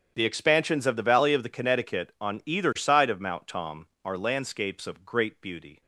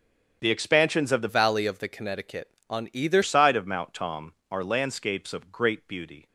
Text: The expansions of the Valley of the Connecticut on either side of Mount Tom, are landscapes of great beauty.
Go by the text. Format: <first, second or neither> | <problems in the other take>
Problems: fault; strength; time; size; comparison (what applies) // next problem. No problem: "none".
first | starts louder than the rest; strong; until 1.4 s; 7.5 dB; strong in the first // changes voice from "Valley" to "either"; from 1.2 to 3.2 s; 2.0 s long